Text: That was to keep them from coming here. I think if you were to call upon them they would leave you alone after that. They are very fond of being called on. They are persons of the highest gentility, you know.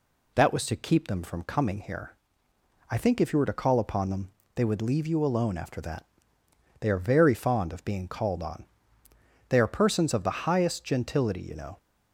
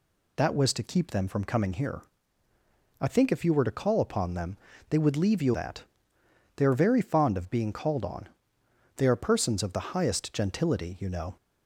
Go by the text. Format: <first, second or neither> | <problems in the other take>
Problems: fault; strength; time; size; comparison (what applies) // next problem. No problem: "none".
first | pauses between "them" and "they"; slight; at 4.5 s; 0.32 s long; slight in the first // skips "alone after"; at 5.5 s